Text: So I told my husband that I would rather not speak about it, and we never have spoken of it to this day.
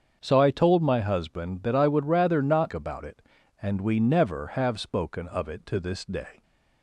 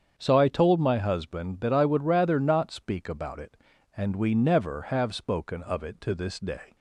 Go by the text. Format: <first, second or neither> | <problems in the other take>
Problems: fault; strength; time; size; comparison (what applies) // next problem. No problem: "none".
second | starts louder than the rest; strong; until 1.2 s; 7 dB; strong in the second // skips "speak"; at 2.7 s